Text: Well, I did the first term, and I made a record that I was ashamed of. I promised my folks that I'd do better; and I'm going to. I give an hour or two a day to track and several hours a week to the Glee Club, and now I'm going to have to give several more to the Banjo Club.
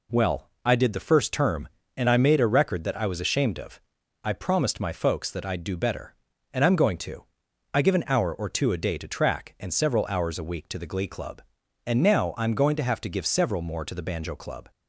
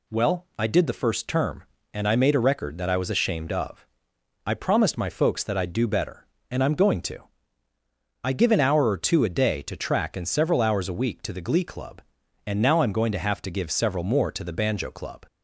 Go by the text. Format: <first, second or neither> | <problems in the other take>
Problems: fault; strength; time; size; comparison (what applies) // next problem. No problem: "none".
neither | none